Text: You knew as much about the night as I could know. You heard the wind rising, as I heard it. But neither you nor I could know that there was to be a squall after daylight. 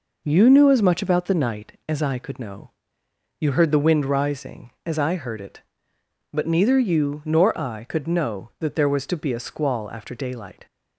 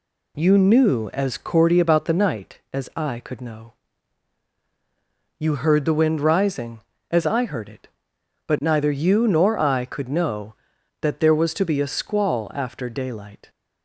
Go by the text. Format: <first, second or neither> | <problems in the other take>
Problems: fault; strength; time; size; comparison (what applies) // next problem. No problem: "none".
first | says "cordy" for "much"; at 1.3 s